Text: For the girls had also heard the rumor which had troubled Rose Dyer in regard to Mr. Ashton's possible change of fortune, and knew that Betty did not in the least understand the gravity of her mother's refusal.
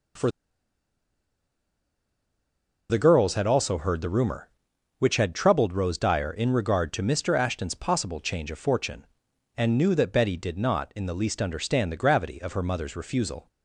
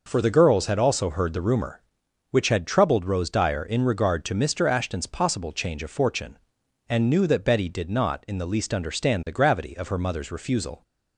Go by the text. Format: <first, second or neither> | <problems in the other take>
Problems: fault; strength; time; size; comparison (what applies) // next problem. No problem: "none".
second | pauses between "For" and "the"; strong; at 0.3 s; 2.5 s long